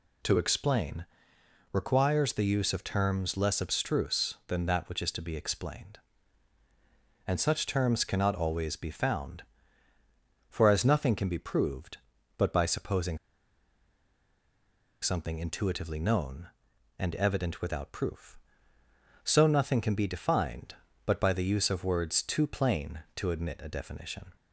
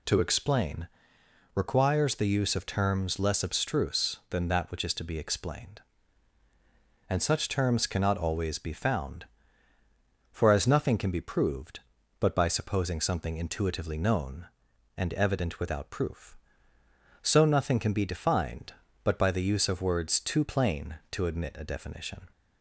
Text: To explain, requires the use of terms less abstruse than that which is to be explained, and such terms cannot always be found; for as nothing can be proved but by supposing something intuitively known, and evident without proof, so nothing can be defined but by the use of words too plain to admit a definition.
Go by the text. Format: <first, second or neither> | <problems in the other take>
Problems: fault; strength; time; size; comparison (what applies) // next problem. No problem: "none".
second | pauses between "supposing" and "something"; strong; at 13.1 s; 1.8 s long